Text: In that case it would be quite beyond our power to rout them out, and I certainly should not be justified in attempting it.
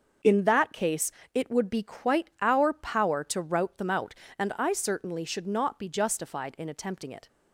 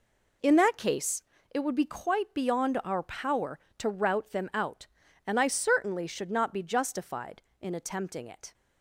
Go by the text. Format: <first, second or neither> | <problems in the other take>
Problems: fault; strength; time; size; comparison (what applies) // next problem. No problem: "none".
second | starts louder than the rest; until 1.4 s; 6.5 dB // pauses between "case" and "it"; slight; at 1.1 s; 0.20 s long; slight in the second // skips "beyond"; at 2.3 s